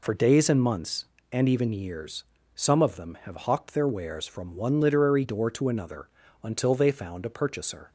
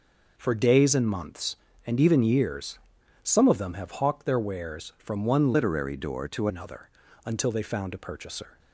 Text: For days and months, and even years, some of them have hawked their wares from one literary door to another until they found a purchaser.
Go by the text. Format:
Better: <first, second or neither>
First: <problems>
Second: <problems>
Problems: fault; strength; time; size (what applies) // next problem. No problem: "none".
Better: first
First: pauses between "another" and "until"; slight; at 6.0 s; 0.34 s long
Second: changes voice from "literary" to "to"; from 5.5 to 6.4 s; 0.9 s long // pauses between "another" and "until"; slight; at 6.8 s; 0.36 s long